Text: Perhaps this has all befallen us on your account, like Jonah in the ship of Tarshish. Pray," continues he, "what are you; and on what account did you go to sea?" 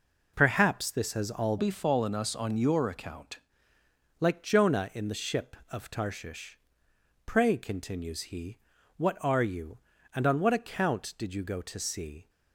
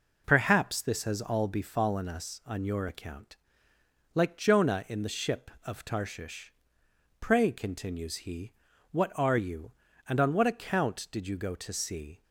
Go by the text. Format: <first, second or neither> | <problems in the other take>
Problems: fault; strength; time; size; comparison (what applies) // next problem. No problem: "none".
second | changes voice from "befallen" to "account"; from 1.5 to 3.3 s; 1.8 s long